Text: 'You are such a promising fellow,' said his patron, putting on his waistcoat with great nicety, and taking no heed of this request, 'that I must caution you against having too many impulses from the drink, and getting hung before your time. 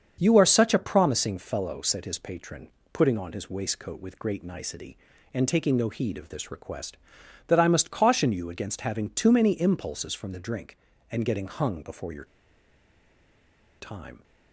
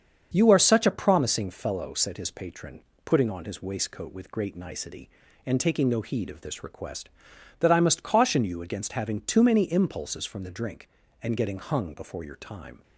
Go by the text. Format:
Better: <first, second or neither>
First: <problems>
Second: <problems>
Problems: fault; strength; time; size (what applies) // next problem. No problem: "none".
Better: second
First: starts louder than the rest; strong; until 1.2 s; 7 dB // pauses between "your" and "time"; strong; at 12.2 s; 1.5 s long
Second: starts louder than the rest; until 1.3 s; 7 dB